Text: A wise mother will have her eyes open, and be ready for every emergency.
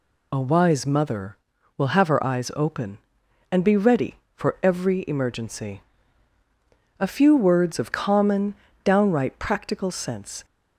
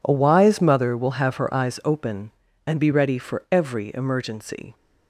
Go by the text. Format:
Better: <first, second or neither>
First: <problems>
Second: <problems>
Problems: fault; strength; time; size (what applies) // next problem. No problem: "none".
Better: second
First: goes on to say "A few words of common downright practical sense"; strong; from 6.9 s on; 3.4 s long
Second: none